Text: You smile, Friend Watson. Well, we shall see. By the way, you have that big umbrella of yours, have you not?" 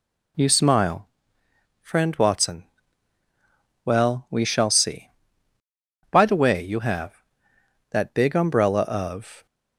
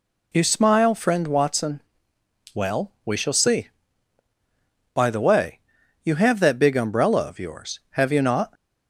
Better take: second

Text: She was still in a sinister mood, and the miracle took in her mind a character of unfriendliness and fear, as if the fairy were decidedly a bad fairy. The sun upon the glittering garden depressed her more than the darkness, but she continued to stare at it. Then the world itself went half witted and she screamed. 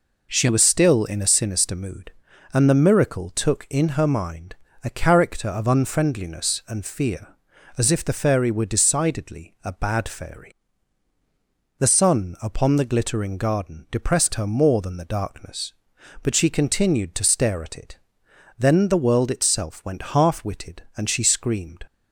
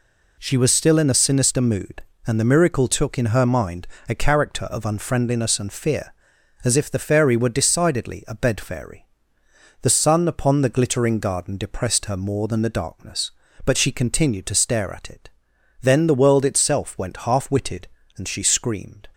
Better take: first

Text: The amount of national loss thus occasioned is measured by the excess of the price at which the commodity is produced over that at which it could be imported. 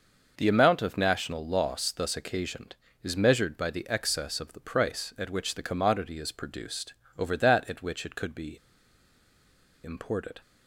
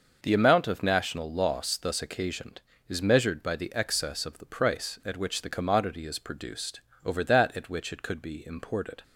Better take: second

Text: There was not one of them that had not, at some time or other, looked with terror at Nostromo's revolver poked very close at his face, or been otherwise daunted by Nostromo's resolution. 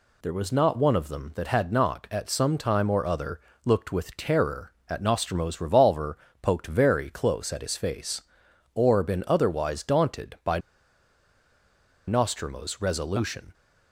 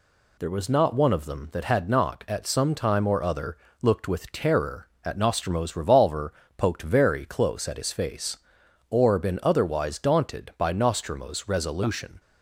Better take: second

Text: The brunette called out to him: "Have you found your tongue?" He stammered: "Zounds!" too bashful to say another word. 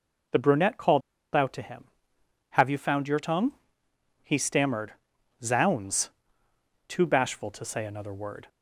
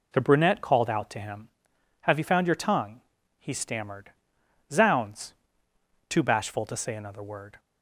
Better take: second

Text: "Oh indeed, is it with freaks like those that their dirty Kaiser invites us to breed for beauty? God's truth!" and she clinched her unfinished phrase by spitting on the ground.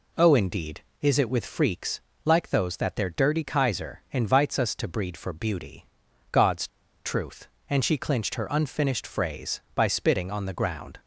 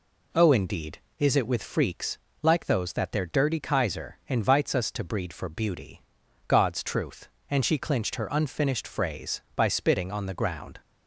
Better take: second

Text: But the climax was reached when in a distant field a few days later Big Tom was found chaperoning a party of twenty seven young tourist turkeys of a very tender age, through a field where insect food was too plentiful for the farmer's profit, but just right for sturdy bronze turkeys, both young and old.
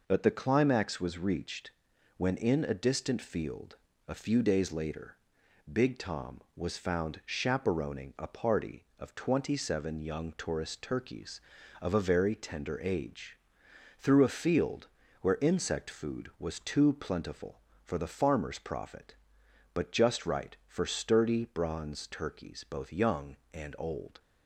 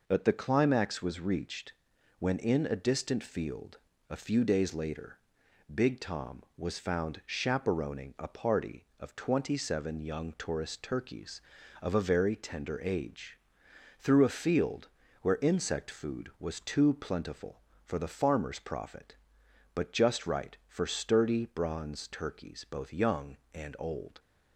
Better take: neither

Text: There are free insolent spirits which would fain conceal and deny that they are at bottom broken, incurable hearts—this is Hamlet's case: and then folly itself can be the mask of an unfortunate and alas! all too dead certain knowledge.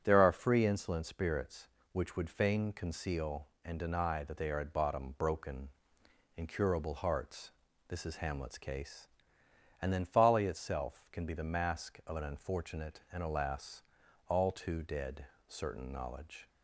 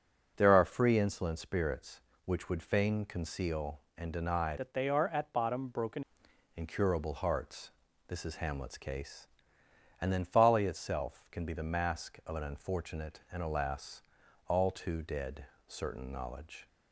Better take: first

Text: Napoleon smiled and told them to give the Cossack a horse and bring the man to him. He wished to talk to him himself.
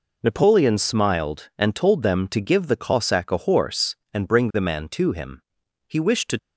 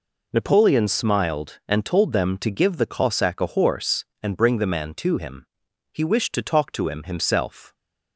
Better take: second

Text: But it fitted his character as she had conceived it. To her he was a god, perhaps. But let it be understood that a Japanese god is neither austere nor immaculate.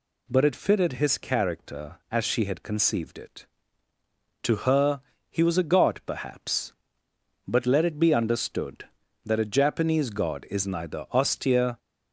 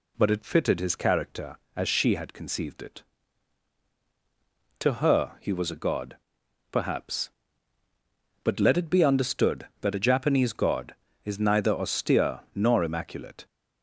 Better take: second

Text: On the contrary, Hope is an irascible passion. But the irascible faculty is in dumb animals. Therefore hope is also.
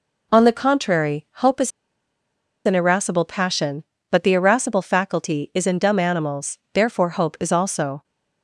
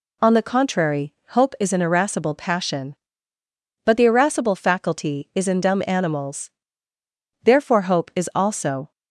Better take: second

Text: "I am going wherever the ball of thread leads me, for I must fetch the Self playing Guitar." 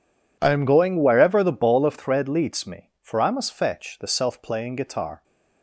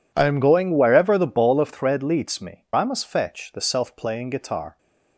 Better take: first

